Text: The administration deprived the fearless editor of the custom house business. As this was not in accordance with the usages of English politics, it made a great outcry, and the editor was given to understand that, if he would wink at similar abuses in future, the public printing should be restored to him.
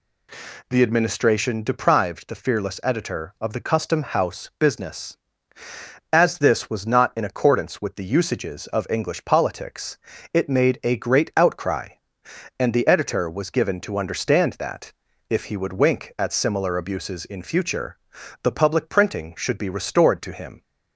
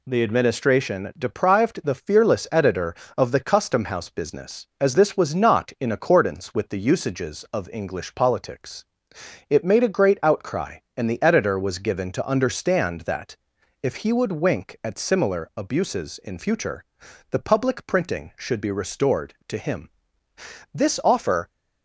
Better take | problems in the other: first | goes on to say "This offer"; noticeable; from 20.7 s on; 0.74 s long

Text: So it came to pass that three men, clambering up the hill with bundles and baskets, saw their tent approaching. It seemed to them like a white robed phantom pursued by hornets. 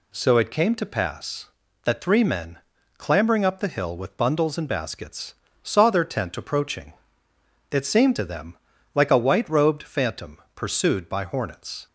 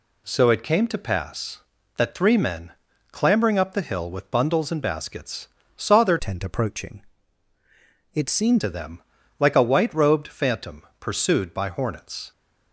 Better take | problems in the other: first | changes voice from "tent" to "seemed"; from 6.1 to 8.6 s; 2.5 s long // pauses between "them" and "like"; slight; at 9.0 s; 0.36 s long; slight in the first // pauses between "phantom" and "pursued"; slight; at 10.8 s; 0.18 s long; slight in the first

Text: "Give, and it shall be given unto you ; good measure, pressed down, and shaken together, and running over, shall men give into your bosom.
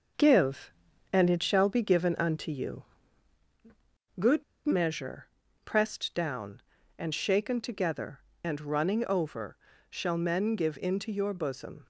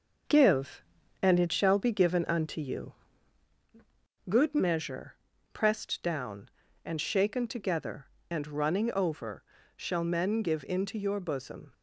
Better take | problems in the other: second | pauses between "good" and "measure"; slight; at 4.4 s; 0.22 s long

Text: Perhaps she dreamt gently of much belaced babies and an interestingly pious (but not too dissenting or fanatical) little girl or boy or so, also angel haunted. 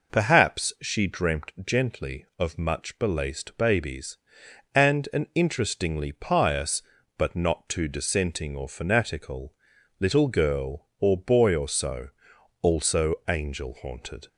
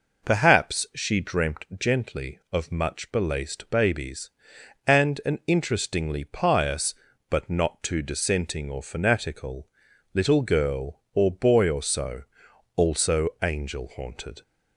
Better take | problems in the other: neither | none

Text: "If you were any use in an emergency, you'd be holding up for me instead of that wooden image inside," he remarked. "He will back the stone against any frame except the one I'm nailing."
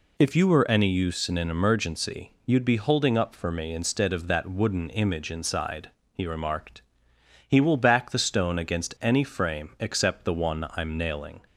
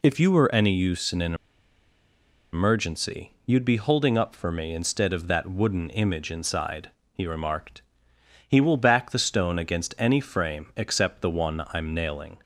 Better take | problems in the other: first | pauses between "an" and "emergency"; at 1.3 s; 1.1 s long

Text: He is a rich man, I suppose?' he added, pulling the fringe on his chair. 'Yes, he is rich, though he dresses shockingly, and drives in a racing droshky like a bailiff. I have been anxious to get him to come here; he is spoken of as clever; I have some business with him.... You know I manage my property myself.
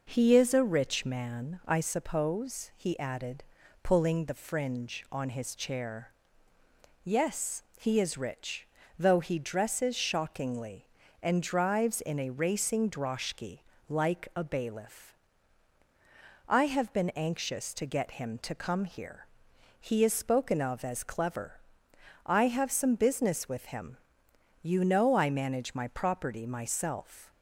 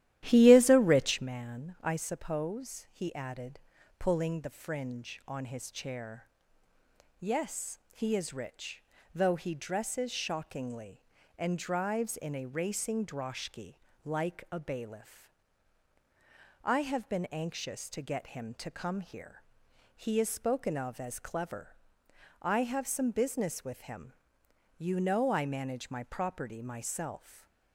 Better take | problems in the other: first | starts louder than the rest; strong; until 1.2 s; 13 dB // pauses between "droshky" and "like"; slight; at 13.7 s; 0.30 s long; slight in the first // stays silent after the last word; slight; from 27.1 s on; 0.6 s long

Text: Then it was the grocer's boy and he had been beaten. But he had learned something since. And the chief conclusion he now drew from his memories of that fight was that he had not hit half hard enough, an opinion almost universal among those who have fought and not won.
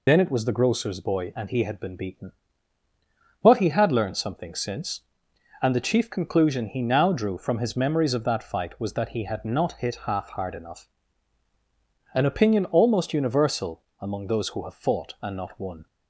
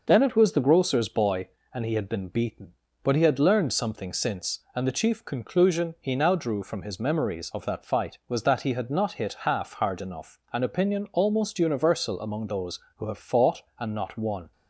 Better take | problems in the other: second | loses the start of "Then"; at 0.0 s; 45 ms // pauses between "universal" and "among"; slight; at 13.8 s; 0.16 s long

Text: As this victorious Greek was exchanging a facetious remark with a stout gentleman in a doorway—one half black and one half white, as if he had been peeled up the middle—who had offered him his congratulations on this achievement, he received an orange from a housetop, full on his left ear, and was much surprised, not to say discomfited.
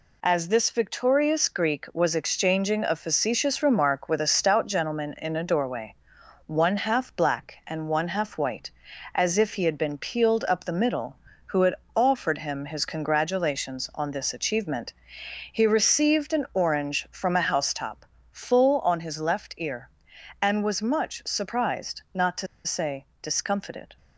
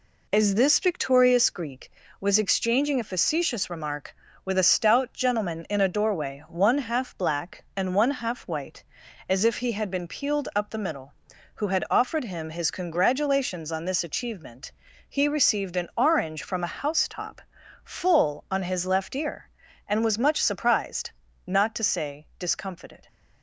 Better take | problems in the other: second | pauses between "had" and "offered"; slight; at 11.7 s; 0.22 s long // pauses between "to" and "say"; slight; at 22.4 s; 0.19 s long // pauses between "say" and "discomfited"; slight; at 23.0 s; 0.18 s long

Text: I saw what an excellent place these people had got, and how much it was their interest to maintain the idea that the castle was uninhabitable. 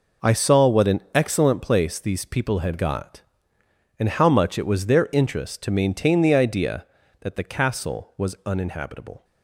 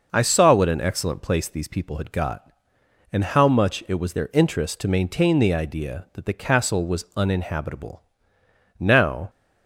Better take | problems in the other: first | goes on to say "Now"; from 8.7 s on; 0.52 s long

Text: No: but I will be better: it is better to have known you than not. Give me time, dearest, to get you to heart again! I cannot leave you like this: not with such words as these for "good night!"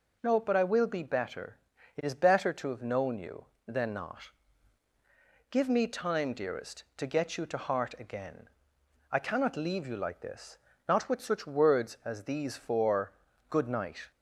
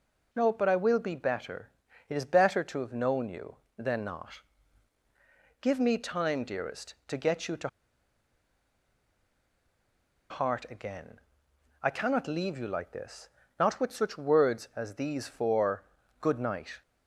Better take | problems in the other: first | pauses between "to" and "heart"; strong; at 7.6 s; 2.6 s long // pauses between "for" and "good"; slight; at 15.8 s; 0.36 s long; slight in the first

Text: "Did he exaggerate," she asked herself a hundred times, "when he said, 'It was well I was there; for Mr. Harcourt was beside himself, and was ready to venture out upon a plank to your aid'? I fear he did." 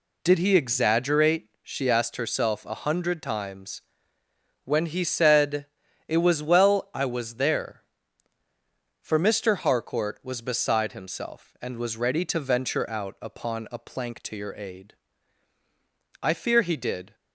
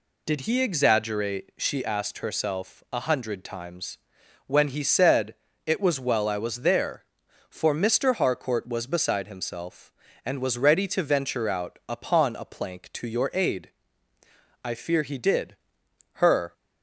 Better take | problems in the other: first | goes on to say "Her"; slight; from 16.1 s on; 0.40 s long

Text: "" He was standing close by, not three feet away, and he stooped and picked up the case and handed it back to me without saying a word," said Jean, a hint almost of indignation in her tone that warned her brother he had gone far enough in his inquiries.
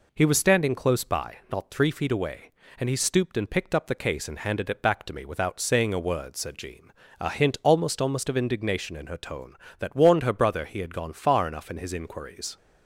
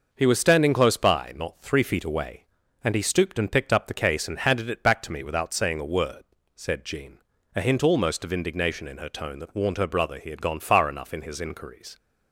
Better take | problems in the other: second | says "almost" twice; at 8.0 s

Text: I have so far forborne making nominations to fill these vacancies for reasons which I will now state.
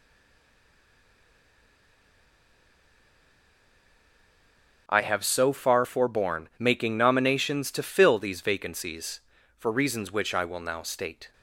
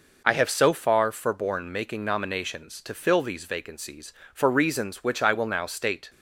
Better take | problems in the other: second | stays silent before the first word; strong; until 4.8 s; 4.8 s long

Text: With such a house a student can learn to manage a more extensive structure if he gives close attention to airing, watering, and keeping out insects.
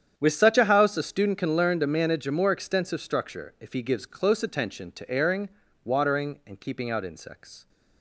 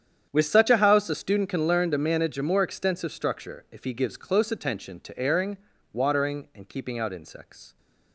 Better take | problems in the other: neither | starts louder than the rest; strong; the same in both

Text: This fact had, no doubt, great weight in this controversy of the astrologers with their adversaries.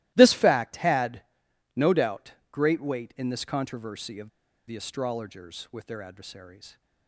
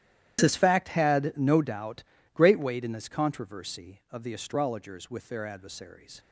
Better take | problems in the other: second | starts louder than the rest; strong; until 1.1 s; 17 dB; strong in the second // pauses between "of" and "the"; at 4.2 s; 0.38 s long

